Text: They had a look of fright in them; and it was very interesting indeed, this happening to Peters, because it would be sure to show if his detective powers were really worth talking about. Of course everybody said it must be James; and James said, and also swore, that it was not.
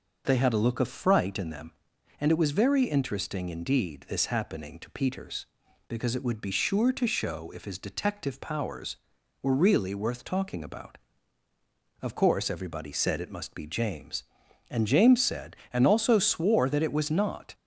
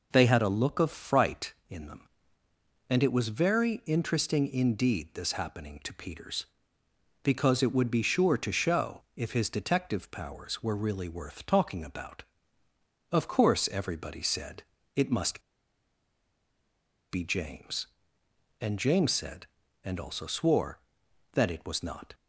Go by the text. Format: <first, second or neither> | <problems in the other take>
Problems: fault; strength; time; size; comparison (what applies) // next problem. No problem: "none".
first | pauses between "said" and "it"; slight; at 14.6 s; 0.34 s long // pauses between "must" and "be"; strong; at 15.4 s; 1.7 s long